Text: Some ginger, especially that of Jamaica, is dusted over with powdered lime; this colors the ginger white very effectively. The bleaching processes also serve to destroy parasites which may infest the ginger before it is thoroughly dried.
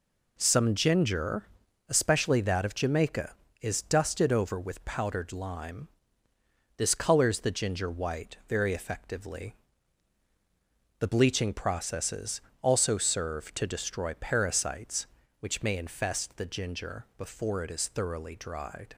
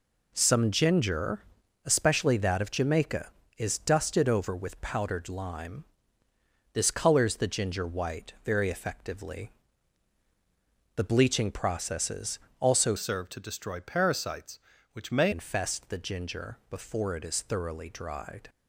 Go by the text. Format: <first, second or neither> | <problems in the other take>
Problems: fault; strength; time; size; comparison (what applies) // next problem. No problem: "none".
first | pauses between "processes" and "also"; slight; at 12.3 s; 0.22 s long; slight in the first // changes voice from "serve" to "may"; from 12.9 to 15.3 s; 2.4 s long